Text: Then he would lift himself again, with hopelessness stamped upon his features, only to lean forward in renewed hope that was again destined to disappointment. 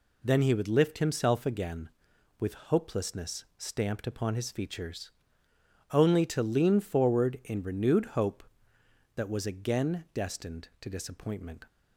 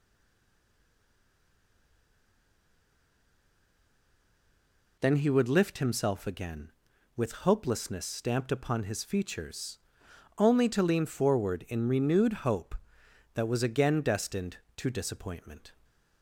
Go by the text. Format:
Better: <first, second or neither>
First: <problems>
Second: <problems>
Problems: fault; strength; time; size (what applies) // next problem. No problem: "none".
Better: first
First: none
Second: stays silent before the first word; strong; until 4.9 s; 4.9 s long